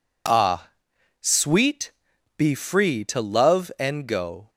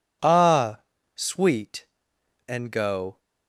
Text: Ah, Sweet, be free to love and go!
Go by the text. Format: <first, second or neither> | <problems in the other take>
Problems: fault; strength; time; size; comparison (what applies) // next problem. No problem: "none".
first | skips "be free to love"; at 2.1 s